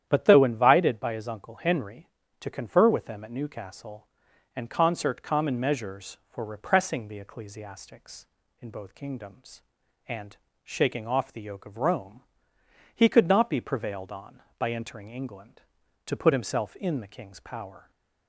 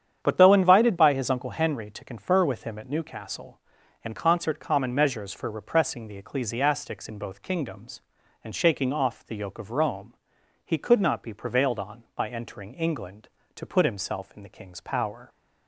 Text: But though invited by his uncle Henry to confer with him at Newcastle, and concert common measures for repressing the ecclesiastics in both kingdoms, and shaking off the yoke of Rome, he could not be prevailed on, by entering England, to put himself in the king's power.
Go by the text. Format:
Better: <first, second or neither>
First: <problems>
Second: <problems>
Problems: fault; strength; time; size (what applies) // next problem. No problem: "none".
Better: second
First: starts louder than the rest; strong; until 1.0 s; 10 dB // says "them" for "him"; at 3.0 s // pauses between "and" and "shaking"; slight; at 10.3 s; 0.28 s long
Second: starts louder than the rest; strong; until 1.2 s; 8.5 dB